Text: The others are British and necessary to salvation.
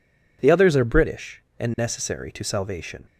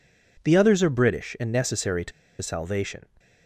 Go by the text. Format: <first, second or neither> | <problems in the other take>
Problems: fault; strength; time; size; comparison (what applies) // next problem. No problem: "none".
first | pauses between "to" and "salvation"; slight; at 2.1 s; 0.30 s long